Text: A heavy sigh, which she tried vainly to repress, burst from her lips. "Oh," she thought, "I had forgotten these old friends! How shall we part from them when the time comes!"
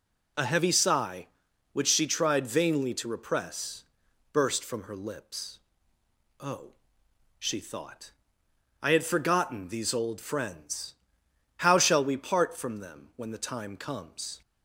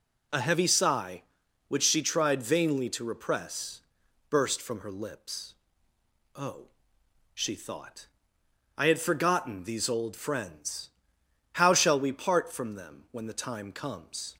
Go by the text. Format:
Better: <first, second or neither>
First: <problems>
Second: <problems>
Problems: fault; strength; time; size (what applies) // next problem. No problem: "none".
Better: neither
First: none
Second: none